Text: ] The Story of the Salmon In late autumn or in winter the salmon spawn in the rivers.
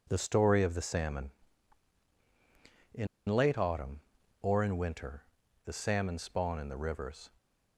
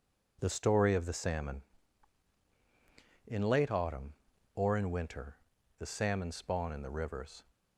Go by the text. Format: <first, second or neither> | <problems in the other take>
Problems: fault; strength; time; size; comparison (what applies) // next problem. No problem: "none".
second | pauses between "In" and "late"; slight; at 3.0 s; 0.22 s long // pauses between "winter" and "the"; at 5.2 s; 0.40 s long; also in the second